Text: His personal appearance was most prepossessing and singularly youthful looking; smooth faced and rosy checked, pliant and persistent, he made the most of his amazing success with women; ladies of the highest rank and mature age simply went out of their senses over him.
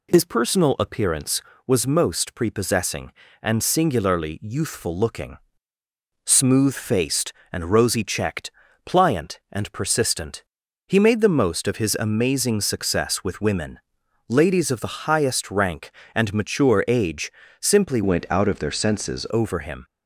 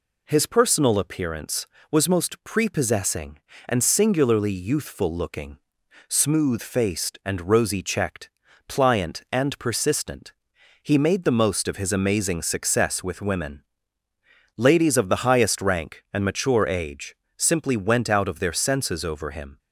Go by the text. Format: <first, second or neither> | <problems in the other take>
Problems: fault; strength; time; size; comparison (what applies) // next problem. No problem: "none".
second | pauses between "age" and "simply"; slight; at 17.2 s; 0.30 s long; slight in the second // changes voice from "went" to "senses"; from 18.0 to 19.2 s; 1.2 s long